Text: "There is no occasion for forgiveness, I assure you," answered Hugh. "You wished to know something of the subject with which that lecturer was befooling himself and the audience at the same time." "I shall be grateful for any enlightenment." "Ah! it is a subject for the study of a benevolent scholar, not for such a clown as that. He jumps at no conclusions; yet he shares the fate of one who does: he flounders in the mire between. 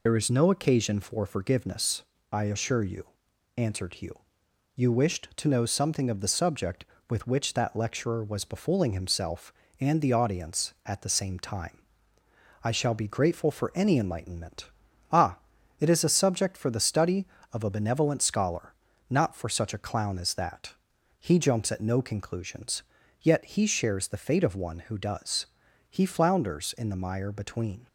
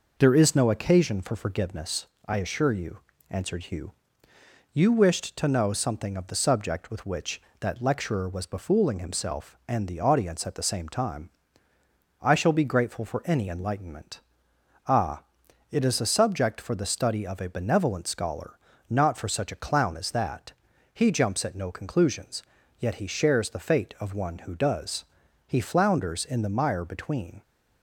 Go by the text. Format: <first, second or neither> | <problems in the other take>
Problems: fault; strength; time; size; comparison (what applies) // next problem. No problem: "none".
second | loses the start of "There"; at 0.0 s; 55 ms